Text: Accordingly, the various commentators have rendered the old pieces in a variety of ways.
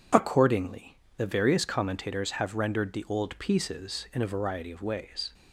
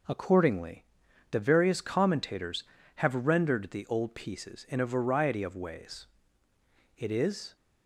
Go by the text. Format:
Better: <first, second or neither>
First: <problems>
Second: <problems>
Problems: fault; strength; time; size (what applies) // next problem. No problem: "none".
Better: first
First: none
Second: goes on to say "It is"; from 6.9 s on; 0.58 s long